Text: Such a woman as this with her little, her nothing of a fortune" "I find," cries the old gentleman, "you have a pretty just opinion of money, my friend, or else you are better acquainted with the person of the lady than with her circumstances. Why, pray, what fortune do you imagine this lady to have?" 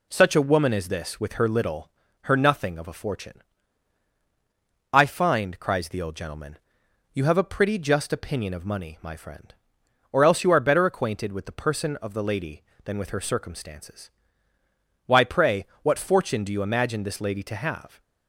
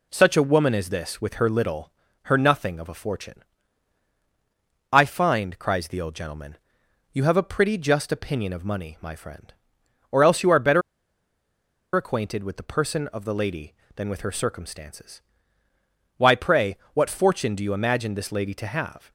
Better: first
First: pauses between "fortune" and "I"; strong; at 3.4 s; 1.4 s long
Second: pauses between "fortune" and "I"; strong; at 3.4 s; 1.4 s long // pauses between "better" and "acquainted"; at 10.8 s; 1.1 s long

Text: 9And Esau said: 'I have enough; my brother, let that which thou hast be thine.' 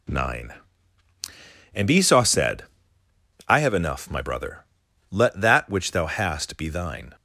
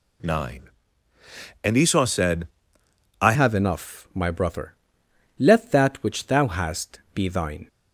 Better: first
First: none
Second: changes voice at "have"; from 3.3 s on; 4.3 s long

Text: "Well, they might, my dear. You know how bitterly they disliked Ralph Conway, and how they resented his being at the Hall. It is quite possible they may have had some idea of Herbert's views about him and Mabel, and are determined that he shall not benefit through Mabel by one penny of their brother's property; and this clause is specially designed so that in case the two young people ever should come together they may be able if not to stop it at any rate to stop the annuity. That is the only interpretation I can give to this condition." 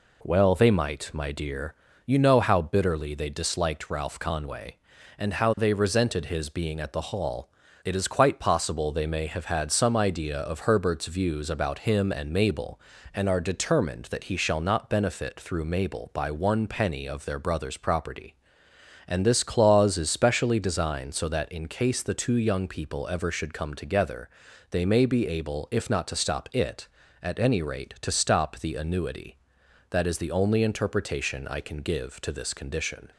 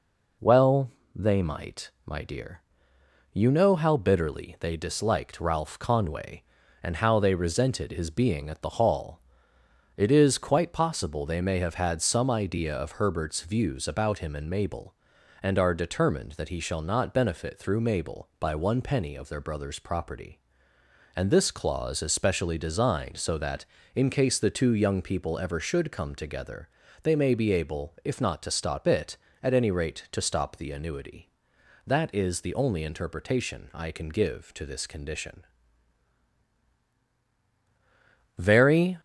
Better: first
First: pauses between "together" and "they"; at 24.2 s; 0.44 s long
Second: pauses between "together" and "they"; slight; at 26.6 s; 0.34 s long // goes on to say "Very"; noticeable; from 38.3 s on; 0.62 s long

